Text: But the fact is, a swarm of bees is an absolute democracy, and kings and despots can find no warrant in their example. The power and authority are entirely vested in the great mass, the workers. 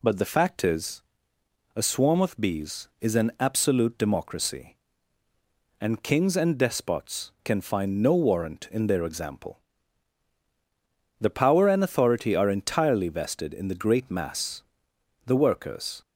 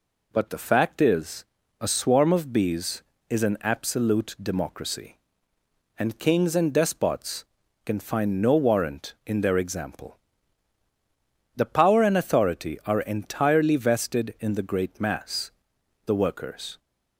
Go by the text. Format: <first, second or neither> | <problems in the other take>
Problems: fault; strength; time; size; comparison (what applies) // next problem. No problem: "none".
neither | none